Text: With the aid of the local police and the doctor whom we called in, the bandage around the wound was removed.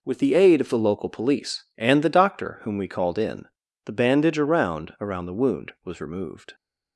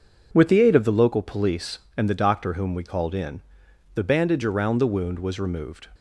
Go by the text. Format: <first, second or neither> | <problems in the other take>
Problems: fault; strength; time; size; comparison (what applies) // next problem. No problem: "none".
second | says "around" twice; at 4.9 s